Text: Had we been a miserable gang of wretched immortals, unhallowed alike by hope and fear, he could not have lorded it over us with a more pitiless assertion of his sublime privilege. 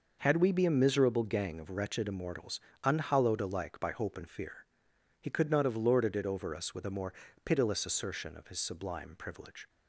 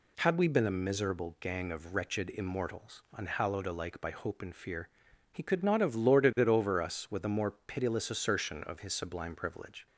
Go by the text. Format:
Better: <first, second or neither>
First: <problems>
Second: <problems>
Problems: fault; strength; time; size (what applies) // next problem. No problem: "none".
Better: second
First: says "be" for "been"; at 0.5 s // pauses between "more" and "pitiless"; slight; at 7.1 s; 0.32 s long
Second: none